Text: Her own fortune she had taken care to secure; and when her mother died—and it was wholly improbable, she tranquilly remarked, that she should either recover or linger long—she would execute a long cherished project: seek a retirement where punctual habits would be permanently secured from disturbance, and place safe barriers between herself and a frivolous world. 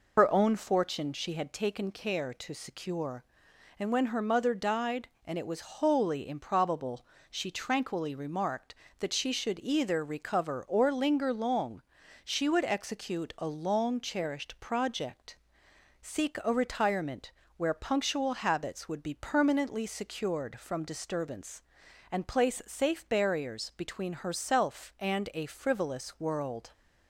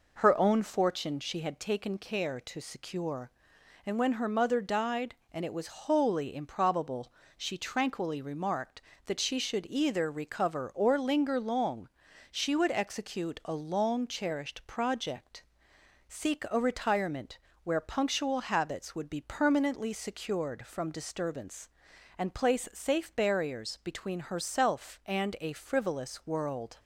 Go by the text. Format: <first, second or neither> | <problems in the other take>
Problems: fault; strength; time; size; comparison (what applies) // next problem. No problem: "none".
second | loses the start of "Her"; at 0.1 s; 80 ms // pauses between "retirement" and "where"; slight; at 17.3 s; 0.26 s long; slight in the second